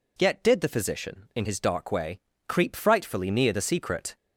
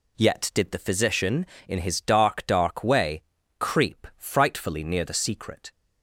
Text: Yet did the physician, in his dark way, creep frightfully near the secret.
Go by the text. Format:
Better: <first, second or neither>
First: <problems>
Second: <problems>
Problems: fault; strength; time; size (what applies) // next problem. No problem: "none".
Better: first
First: none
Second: says "dark" twice; at 2.4 s